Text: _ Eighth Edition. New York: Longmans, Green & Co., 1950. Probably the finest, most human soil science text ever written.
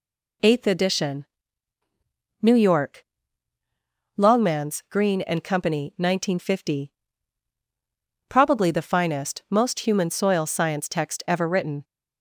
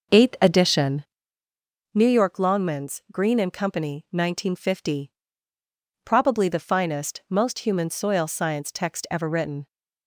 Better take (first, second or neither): first